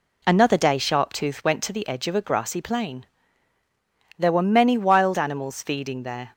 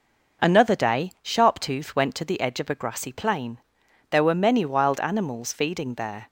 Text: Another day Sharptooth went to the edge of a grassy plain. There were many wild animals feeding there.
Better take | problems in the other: neither | none

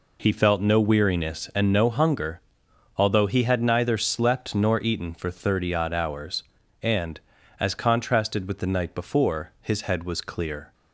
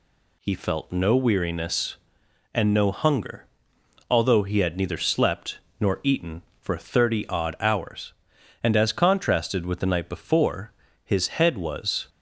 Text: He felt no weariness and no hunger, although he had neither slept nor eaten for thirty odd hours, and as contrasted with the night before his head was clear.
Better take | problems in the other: first | pauses between "slept" and "nor"; slight; at 5.5 s; 0.22 s long // pauses between "before" and "his"; slight; at 10.7 s; 0.30 s long // stops before "clear"; at 12.0 s

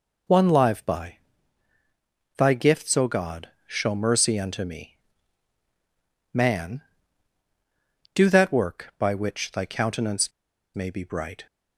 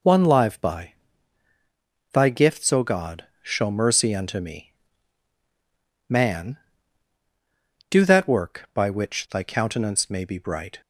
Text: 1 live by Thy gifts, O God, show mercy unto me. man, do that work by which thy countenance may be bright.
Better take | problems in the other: second | pauses between "by" and "Thy"; at 1.1 s; 1.1 s long; also in the second // pauses between "countenance" and "may"; at 10.3 s; 0.44 s long

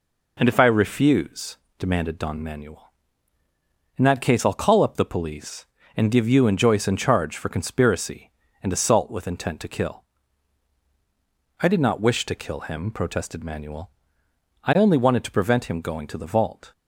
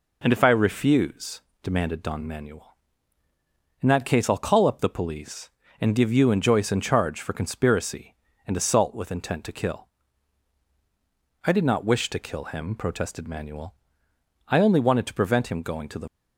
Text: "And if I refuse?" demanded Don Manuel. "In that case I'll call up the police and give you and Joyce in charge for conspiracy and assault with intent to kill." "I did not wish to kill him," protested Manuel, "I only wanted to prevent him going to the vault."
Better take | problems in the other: first | stops before "vault"; at 16.0 s

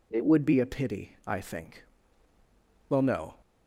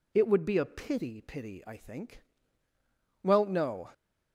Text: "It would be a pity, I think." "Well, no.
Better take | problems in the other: first | says "pity" twice; at 1.2 s

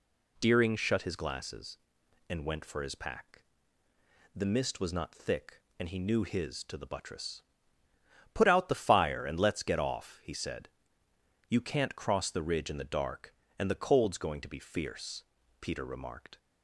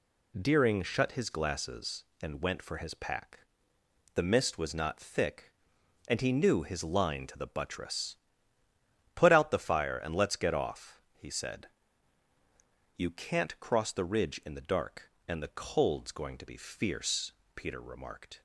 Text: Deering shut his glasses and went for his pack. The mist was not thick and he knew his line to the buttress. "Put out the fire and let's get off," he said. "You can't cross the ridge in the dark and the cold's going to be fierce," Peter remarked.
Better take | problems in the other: second | skips "line"; at 6.6 s

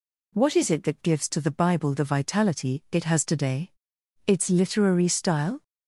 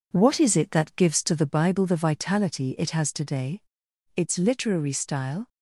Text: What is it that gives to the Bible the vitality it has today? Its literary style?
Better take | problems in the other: first | gets quieter; noticeable; throughout; 5.5 dB

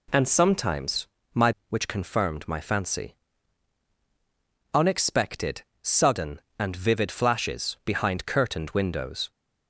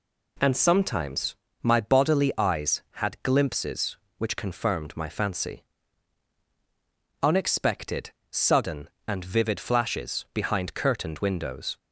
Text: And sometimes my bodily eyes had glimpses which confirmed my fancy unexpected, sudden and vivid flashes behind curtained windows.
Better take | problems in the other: second | pauses between "sometimes" and "my"; slight; at 1.0 s; 0.26 s long; slight in the second // skips "bodily eyes had glimpses"; at 1.6 s // pauses between "fancy" and "unexpected"; strong; at 3.1 s; 1.5 s long; strong in the second

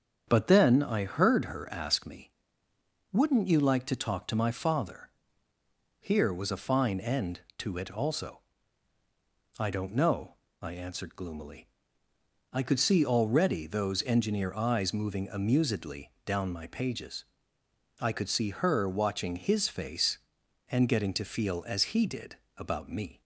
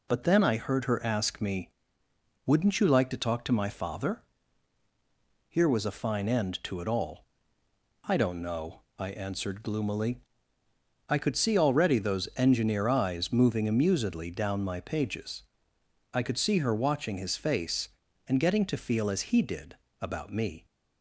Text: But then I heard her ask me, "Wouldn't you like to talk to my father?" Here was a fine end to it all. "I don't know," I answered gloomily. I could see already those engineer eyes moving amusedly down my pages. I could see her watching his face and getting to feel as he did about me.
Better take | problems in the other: second | starts louder than the rest; strong; until 1.2 s; 7.5 dB // says "also" for "all"; at 7.9 s // pauses between "amusedly" and "down"; slight; at 16.1 s; 0.16 s long // pauses between "did" and "about"; slight; at 22.3 s; 0.20 s long; slight in the second

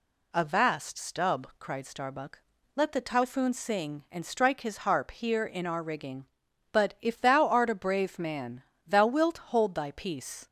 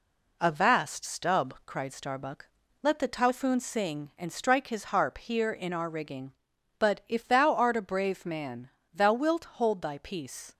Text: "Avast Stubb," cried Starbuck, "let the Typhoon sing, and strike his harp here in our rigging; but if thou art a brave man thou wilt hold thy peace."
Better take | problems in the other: first | gets quieter; slight; throughout; 3.5 dB // pauses between "man" and "thou"; slight; at 8.6 s; 0.24 s long; slight in the first

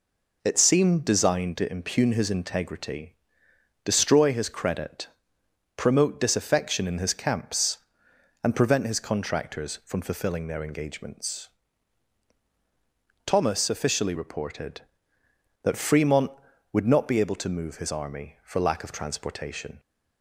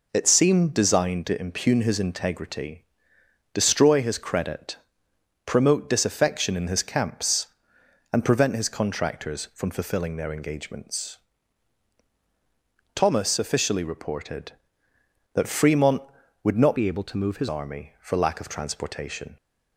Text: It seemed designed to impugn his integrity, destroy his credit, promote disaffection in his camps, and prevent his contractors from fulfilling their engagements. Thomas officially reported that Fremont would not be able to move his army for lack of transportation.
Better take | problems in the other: first | changes voice from "be" to "his"; from 16.7 to 17.4 s; 0.7 s long

